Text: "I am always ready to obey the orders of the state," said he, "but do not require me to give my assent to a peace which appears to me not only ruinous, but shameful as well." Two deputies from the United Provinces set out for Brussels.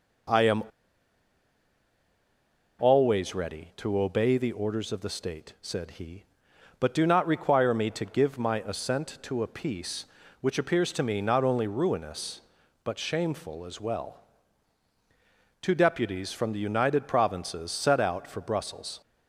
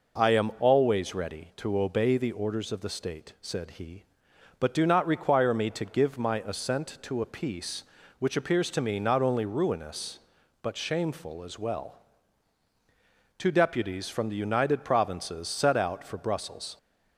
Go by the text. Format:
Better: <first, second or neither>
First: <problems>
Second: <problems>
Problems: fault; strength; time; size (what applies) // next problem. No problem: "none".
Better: second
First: pauses between "am" and "always"; strong; at 0.6 s; 2.1 s long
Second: none